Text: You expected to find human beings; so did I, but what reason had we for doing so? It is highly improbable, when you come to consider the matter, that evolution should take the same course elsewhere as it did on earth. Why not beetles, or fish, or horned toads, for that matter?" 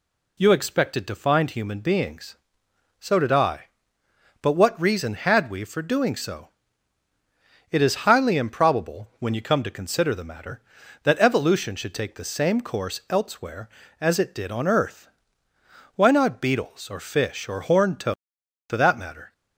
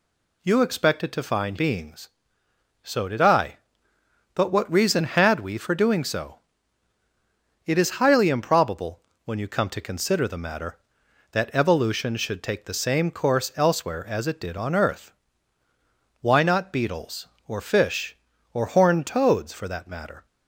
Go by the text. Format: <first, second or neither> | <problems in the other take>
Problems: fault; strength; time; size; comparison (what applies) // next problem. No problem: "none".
first | skips "human"; at 1.5 s